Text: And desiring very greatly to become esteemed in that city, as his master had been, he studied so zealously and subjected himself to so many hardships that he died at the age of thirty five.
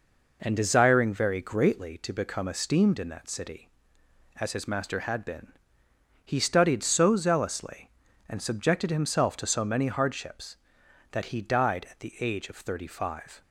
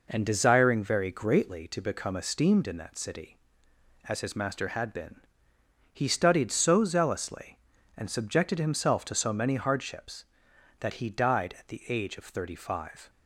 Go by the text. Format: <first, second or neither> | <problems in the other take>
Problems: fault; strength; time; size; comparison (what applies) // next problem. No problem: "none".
neither | none